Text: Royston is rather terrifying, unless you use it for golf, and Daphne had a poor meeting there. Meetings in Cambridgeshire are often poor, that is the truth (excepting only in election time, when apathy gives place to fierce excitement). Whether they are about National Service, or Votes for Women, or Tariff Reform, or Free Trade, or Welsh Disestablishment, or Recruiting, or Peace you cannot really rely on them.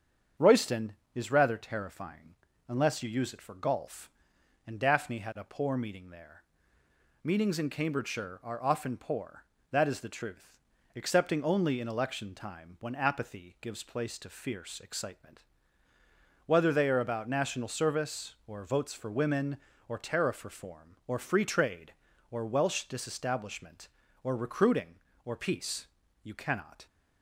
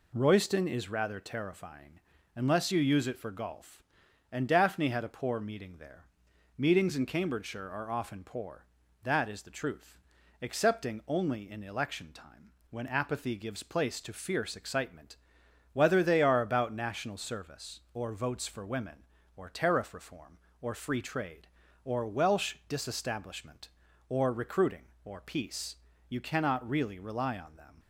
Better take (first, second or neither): second